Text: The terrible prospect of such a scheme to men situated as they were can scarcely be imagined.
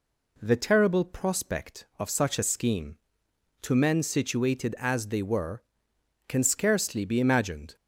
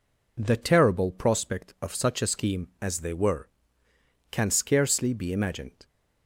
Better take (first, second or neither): first